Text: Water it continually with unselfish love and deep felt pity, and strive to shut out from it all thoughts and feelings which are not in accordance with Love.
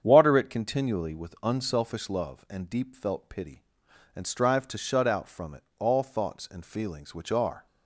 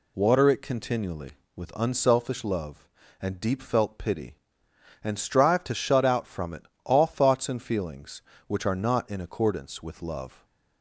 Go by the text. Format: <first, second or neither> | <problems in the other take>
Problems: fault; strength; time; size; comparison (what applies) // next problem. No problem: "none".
second | starts louder than the rest; strong; until 1.0 s; 8 dB // pauses between "it" and "all"; slight; at 5.6 s; 0.16 s long; slight in the second // stops before "not in accordance with Love"; at 7.6 s